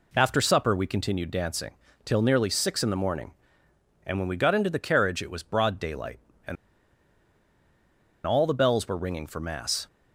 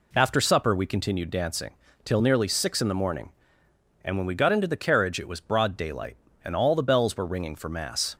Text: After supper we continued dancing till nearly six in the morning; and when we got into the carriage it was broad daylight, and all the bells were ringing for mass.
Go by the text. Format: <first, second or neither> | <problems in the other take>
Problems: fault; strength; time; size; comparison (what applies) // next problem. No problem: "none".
second | pauses between "dancing" and "till"; slight; at 1.7 s; 0.30 s long; slight in the second // pauses between "and" and "all"; strong; at 6.5 s; 1.7 s long